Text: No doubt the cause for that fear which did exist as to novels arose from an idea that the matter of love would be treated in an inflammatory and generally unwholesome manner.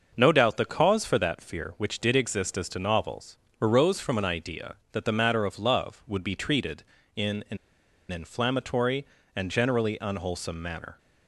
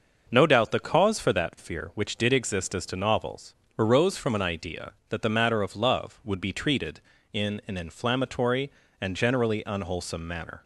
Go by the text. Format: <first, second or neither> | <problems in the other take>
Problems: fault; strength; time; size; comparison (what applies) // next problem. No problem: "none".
second | starts louder than the rest; until 1.1 s; 6 dB; noticeable in the second // pauses between "novels" and "arose"; slight; at 3.3 s; 0.24 s long; slight in the second // pauses between "an" and "inflammatory"; noticeable; at 7.5 s; 0.54 s long